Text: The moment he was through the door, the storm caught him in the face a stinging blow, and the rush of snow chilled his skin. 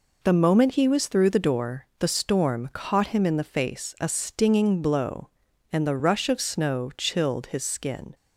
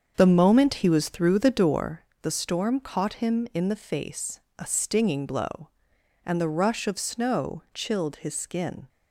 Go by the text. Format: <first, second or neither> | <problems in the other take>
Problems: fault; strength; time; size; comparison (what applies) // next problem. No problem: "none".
first | starts louder than the rest; until 1.9 s; 7 dB // pauses between "face" and "a"; slight; at 4.4 s; 0.18 s long